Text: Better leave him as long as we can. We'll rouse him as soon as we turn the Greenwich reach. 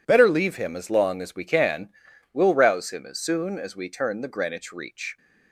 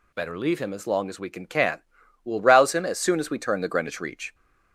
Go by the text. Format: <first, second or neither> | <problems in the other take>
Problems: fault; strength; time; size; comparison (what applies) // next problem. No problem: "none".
first | says "can" twice; at 1.4 s